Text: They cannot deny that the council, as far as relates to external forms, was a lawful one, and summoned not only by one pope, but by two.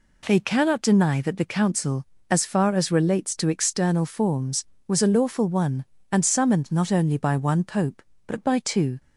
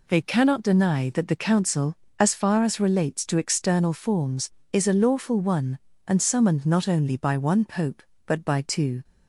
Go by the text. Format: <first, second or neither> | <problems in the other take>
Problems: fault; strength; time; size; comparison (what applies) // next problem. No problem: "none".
first | says "is" for "was"; at 4.7 s